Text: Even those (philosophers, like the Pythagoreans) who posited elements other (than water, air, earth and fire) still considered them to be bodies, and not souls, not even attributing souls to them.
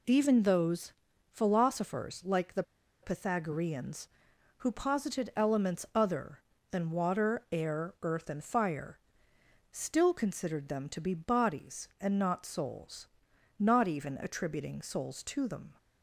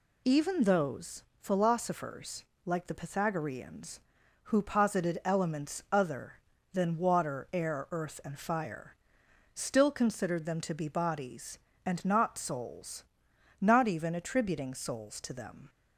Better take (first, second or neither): second